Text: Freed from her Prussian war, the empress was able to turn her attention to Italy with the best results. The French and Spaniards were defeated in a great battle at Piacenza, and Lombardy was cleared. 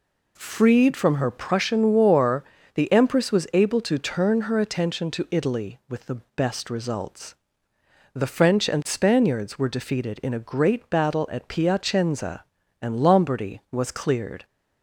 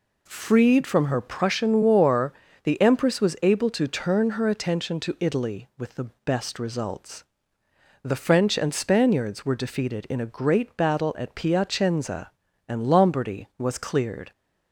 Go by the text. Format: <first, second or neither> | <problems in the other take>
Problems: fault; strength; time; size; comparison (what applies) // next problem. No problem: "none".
neither | none